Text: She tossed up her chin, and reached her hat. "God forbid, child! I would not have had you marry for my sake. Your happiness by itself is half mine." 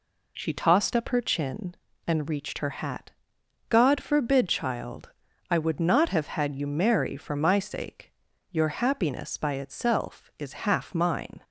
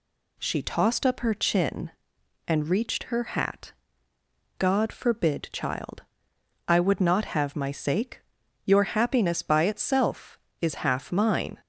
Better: first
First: none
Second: skips "had you marry for"; at 7.5 s

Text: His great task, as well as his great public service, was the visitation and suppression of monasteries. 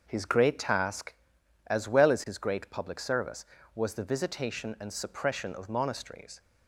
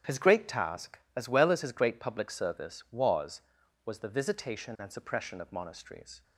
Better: first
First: starts louder than the rest; until 1.0 s; 6.5 dB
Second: starts louder than the rest; strong; until 1.2 s; 9.5 dB // says "was" twice; at 3.8 s

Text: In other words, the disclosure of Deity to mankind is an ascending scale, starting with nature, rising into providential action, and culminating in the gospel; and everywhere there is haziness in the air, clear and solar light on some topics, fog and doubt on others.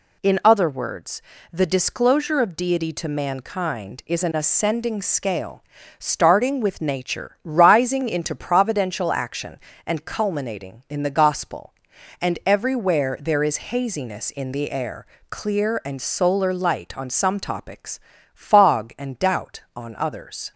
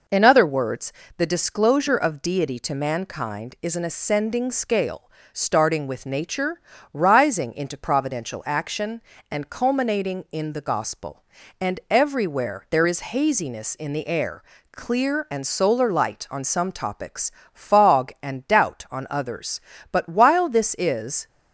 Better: first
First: none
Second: goes on to say "But while this is"; from 19.8 s on; 1.3 s long

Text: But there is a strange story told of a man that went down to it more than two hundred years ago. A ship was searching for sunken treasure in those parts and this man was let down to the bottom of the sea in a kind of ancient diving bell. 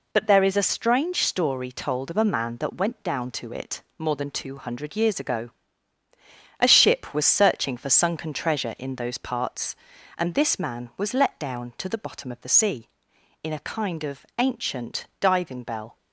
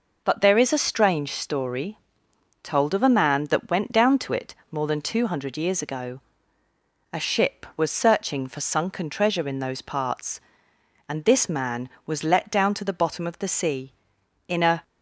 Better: first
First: pauses between "it" and "more"; slight; at 3.8 s; 0.16 s long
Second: pauses between "story" and "told"; noticeable; at 1.9 s; 0.66 s long // pauses between "it" and "more"; slight; at 4.5 s; 0.16 s long // stops before "kind of ancient diving bell"; at 14.8 s

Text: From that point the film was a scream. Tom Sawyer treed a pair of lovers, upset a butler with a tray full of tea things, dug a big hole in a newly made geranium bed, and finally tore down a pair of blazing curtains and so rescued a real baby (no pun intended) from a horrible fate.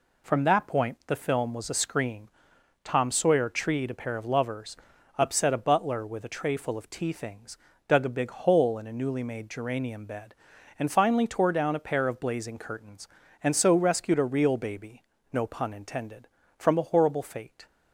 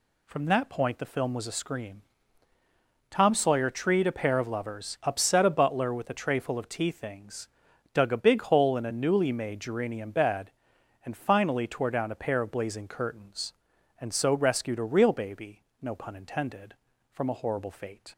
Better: neither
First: none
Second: none

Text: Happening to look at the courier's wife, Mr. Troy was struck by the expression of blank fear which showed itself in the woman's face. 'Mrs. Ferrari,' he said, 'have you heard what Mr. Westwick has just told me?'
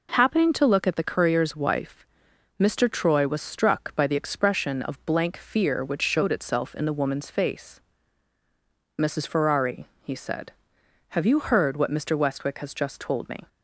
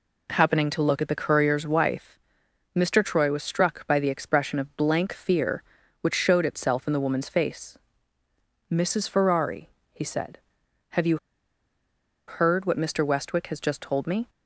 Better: first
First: none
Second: pauses between "you" and "heard"; at 11.1 s; 1.1 s long

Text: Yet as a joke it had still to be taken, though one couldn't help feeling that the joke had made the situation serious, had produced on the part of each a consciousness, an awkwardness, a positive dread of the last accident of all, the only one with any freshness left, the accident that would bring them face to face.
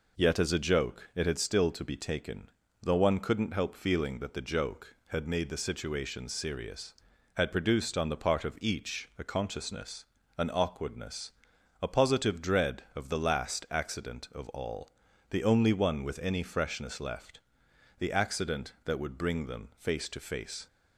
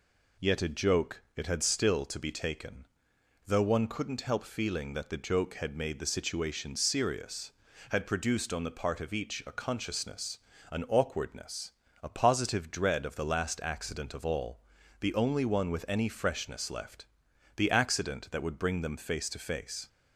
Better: first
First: none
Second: skips "as"; at 0.6 s

